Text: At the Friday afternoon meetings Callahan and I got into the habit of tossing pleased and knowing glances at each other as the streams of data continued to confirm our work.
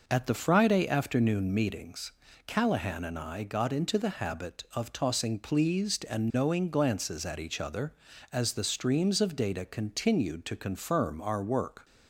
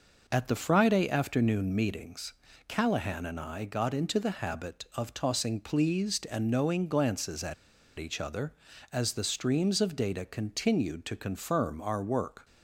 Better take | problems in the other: first | pauses between "meetings" and "Callahan"; slight; at 2.3 s; 0.34 s long; slight in the first // pauses between "at" and "each"; at 7.5 s; 0.44 s long

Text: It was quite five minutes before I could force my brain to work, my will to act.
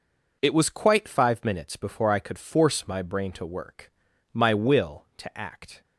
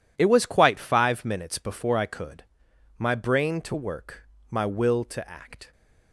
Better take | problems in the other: first | skips "force"; at 2.7 s

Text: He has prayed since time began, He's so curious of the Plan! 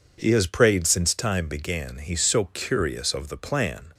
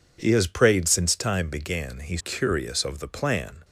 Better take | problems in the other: first | skips "so"; at 2.1 s

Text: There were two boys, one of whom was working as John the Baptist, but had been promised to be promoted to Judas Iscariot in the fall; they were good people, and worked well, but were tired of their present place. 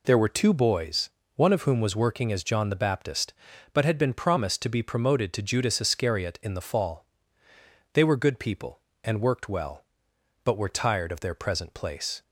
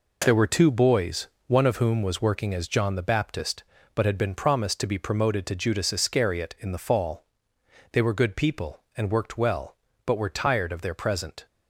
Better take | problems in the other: first | stops before "place"; at 11.4 s

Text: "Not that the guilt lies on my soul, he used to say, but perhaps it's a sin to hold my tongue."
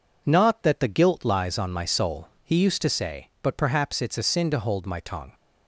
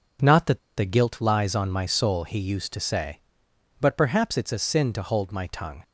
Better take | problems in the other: first | pauses between "that" and "the"; slight; at 0.5 s; 0.18 s long

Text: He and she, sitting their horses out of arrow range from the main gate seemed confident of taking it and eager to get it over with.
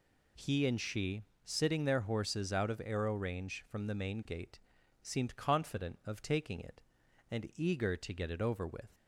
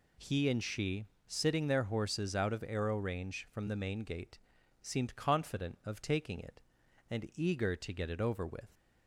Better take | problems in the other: neither | pauses between "gate" and "seemed"; the same in both

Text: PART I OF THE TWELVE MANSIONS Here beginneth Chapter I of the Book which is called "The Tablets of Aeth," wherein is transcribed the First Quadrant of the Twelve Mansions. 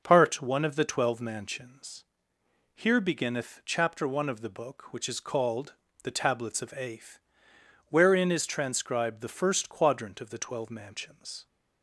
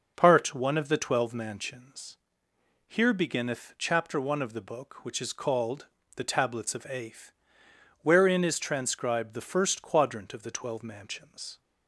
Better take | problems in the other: neither | pauses between "MANSIONS" and "Here"; noticeable; the same in both // pauses between "called" and "The"; slight; the same in both

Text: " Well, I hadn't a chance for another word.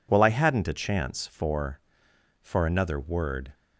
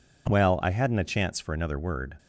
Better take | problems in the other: second | says "for" twice; at 2.4 s

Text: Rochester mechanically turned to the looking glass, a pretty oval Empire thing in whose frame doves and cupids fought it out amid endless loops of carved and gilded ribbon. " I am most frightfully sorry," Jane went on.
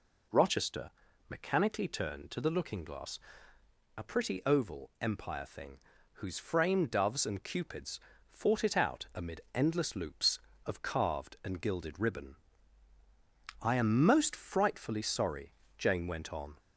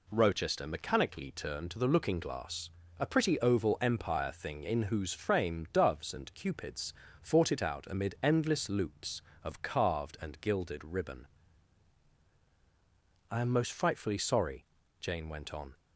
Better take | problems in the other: second | pauses between "Rochester" and "mechanically"; at 0.9 s; 0.40 s long // skips "in"; at 5.9 s // pauses between "cupids" and "fought"; slight; at 7.9 s; 0.30 s long; slight in the second

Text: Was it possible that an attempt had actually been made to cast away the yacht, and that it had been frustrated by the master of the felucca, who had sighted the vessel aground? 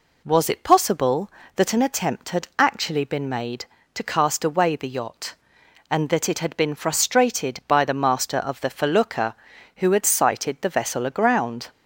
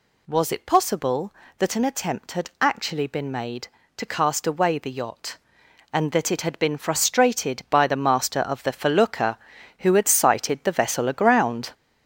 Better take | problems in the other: first | gets louder; throughout; 6 dB

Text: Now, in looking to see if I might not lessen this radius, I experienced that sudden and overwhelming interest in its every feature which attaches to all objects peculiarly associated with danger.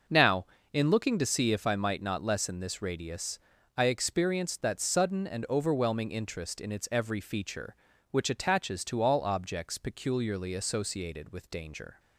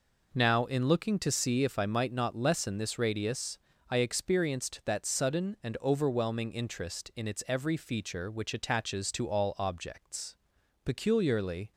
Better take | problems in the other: first | pauses between "objects" and "peculiarly"; noticeable; at 10.3 s; 0.48 s long // stops before "associated with danger"; at 11.7 s

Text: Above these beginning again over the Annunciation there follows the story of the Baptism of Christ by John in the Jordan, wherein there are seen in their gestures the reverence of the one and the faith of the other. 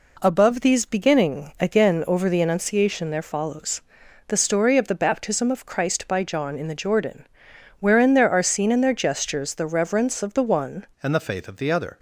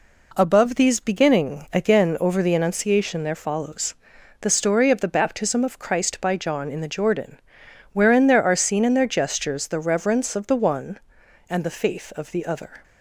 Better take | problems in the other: second | pauses between "follows" and "the"; noticeable; at 3.8 s; 0.46 s long; noticeable in the second // changes voice at "and"; from 11.0 s on; 0.9 s long

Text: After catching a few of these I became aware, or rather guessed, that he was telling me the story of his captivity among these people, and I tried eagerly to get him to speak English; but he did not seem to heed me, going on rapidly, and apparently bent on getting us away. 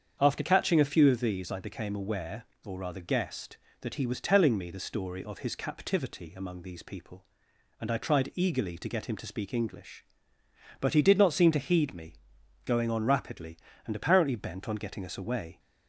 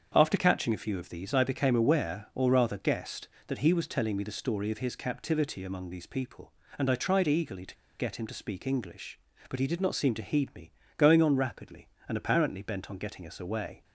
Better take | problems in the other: first | starts louder than the rest; strong; until 1.1 s; 7.5 dB; strong in the first // pauses between "to" and "get"; slight; at 7.7 s; 0.23 s long

